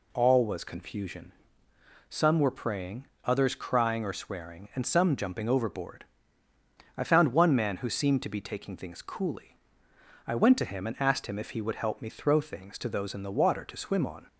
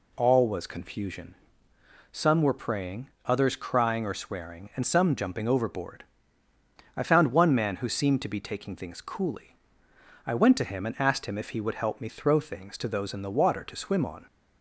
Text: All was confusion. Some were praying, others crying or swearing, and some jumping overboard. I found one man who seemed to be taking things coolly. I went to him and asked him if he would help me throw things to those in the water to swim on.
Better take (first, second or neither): neither